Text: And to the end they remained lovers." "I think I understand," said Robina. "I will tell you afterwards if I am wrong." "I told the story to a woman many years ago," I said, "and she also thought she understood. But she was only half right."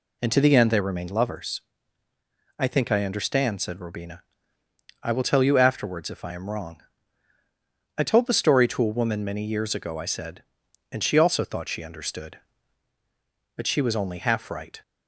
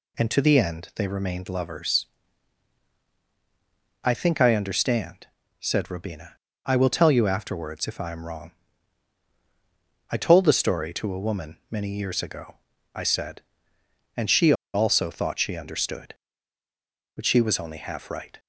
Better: first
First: none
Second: pauses between "she" and "also"; slight; at 14.5 s; 0.21 s long

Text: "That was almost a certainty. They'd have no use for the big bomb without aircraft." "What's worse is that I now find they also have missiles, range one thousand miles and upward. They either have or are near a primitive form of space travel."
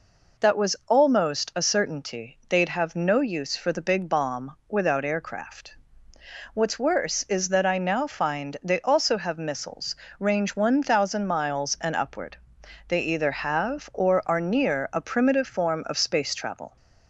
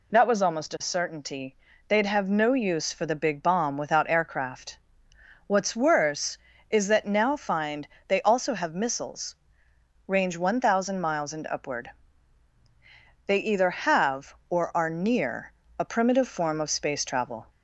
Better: first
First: none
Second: skips "I"; at 7.0 s // pauses between "find" and "they"; slight; at 7.8 s; 0.18 s long // pauses between "near" and "a"; slight; at 15.5 s; 0.28 s long

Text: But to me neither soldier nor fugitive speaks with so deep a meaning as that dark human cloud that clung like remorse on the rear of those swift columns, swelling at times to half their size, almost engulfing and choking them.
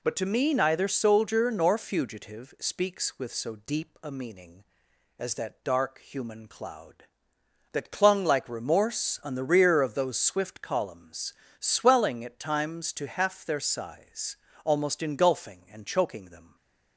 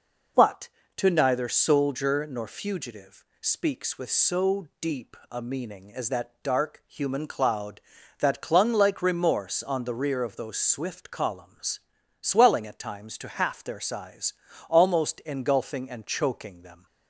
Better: first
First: none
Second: skips "me"; at 1.0 s // pauses between "fugitive" and "speaks"; slight; at 3.2 s; 0.16 s long // pauses between "deep" and "a"; slight; at 5.1 s; 0.16 s long

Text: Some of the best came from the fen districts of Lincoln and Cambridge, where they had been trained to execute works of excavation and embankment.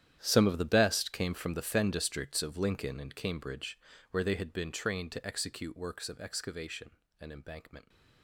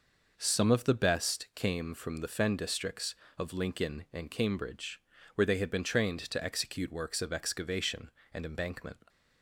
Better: second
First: gets quieter; strong; throughout; 16.5 dB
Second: none

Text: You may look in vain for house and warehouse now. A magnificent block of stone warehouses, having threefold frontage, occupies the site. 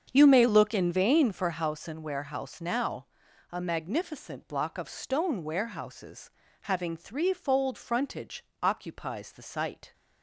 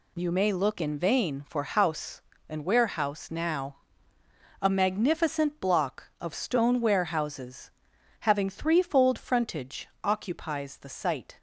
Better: second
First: starts louder than the rest; strong; until 1.7 s; 7.5 dB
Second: none

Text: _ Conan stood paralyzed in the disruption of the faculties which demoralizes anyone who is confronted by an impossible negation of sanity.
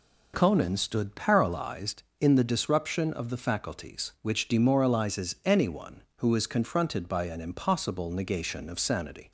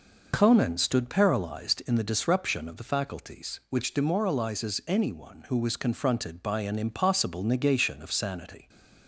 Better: first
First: none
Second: says "was" for "is"; at 5.5 s

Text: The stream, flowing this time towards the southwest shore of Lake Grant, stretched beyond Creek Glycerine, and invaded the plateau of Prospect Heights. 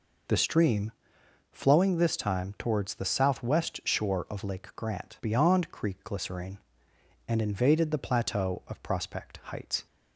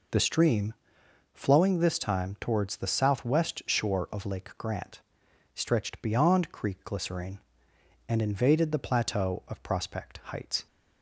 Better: second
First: skips "stretched"; at 5.2 s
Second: none

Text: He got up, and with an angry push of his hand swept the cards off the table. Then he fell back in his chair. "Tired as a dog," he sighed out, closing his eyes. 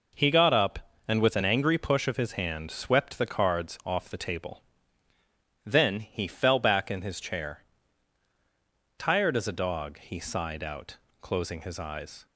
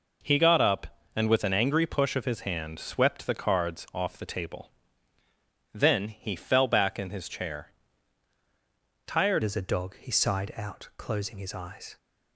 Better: first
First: none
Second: changes voice at "as"; from 9.4 s on; 2.5 s long

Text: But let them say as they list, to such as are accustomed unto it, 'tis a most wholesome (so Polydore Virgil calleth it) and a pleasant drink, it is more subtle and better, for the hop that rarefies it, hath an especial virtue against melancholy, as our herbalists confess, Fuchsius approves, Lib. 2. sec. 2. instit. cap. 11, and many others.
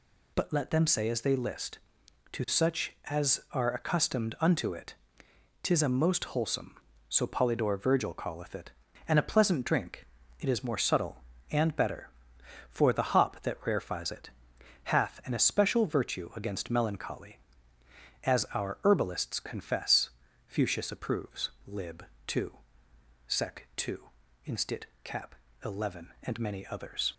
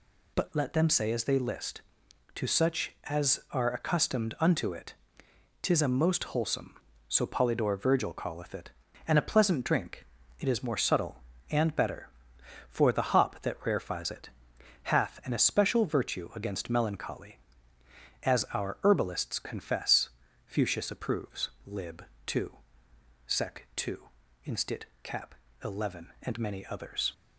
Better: neither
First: none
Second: none

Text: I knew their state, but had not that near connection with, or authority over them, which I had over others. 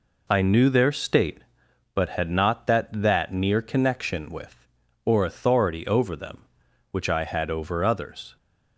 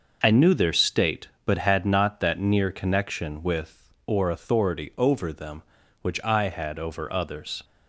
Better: second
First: says "that" twice; at 2.9 s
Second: none

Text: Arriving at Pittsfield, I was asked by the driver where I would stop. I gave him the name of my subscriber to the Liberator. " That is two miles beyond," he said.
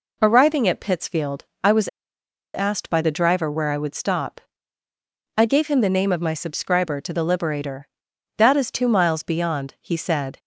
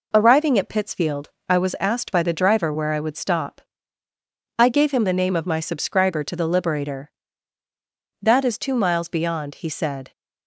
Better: second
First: pauses between "was" and "asked"; noticeable; at 1.8 s; 0.68 s long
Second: none

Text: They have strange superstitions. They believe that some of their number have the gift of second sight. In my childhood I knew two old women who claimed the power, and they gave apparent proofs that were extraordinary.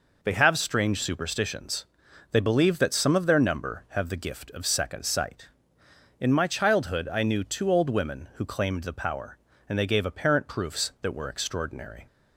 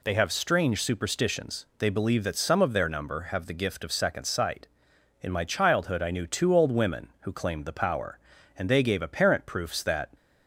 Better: first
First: none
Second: stops before "were extraordinary"; at 10.1 s

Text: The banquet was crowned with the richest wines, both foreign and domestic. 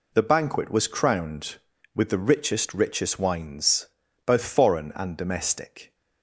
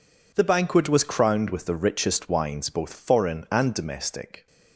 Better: second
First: says "richest" twice; at 2.7 s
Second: none

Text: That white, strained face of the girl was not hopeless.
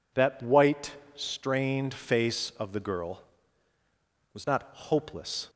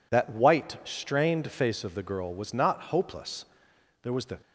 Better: first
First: none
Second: goes on to say "There was the"; slight; from 4.0 s on; 0.36 s long

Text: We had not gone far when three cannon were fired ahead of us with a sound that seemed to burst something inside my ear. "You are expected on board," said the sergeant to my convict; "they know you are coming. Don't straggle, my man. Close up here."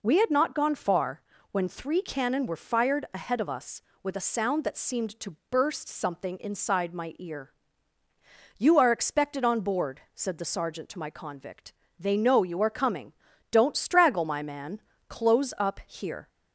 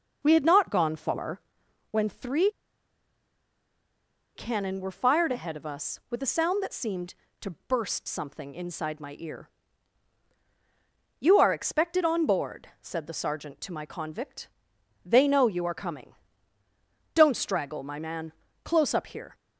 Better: first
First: pauses between "far" and "when"; slight; at 1.2 s; 0.30 s long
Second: pauses between "far" and "when"; noticeable; at 1.4 s; 0.50 s long // pauses between "three" and "cannon"; strong; at 2.4 s; 1.8 s long

